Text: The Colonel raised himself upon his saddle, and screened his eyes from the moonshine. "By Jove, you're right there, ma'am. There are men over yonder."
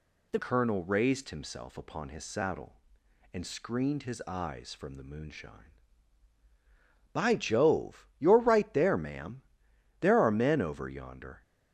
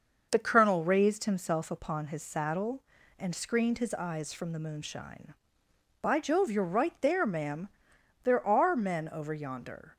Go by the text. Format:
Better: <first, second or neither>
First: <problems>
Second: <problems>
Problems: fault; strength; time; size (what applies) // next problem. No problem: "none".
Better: second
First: changes voice at "Colonel"; from 0.4 s on; 11.0 s long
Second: none